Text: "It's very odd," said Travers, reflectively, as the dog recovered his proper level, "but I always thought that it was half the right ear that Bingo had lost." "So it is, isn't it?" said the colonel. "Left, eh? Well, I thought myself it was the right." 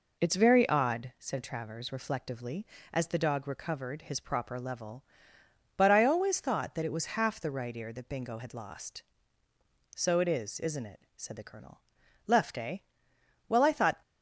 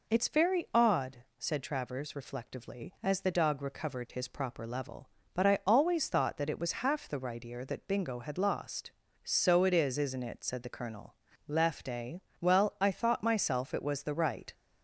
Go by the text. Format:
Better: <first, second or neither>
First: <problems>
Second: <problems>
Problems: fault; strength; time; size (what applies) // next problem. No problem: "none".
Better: second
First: stops before "myself it was the right"; at 14.0 s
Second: none